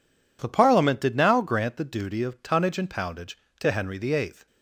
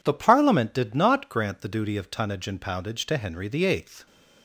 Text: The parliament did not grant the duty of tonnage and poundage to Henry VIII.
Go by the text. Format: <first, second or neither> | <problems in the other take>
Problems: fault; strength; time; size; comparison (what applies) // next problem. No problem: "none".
second | says "now" for "not"; at 1.1 s